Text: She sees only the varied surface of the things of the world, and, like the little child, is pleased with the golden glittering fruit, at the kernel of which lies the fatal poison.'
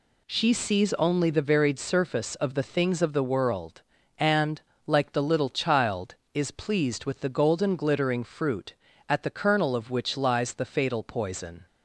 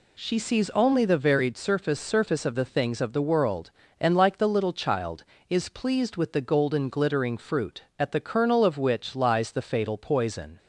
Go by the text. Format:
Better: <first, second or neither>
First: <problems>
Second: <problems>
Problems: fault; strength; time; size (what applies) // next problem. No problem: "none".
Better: first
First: none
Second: says "surface" twice; at 1.9 s